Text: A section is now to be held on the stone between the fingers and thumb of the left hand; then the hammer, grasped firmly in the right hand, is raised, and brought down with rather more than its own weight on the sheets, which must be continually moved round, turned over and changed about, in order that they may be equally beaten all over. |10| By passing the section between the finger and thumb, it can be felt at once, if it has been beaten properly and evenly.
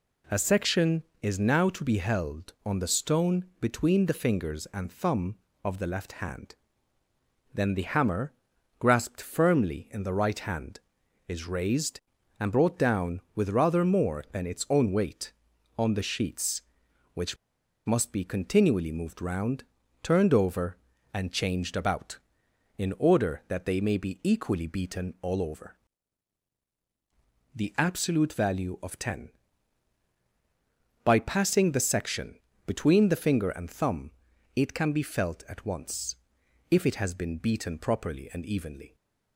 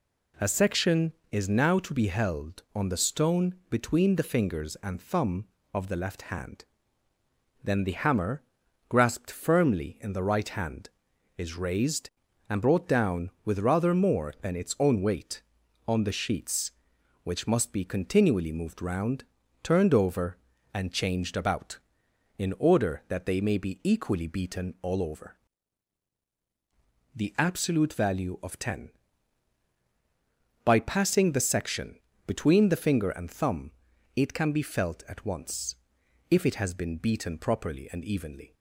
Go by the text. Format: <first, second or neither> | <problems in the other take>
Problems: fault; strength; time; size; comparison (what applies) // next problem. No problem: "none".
second | pauses between "which" and "must"; noticeable; at 17.3 s; 0.50 s long // pauses between "section" and "between"; slight; at 32.3 s; 0.26 s long; slight in the second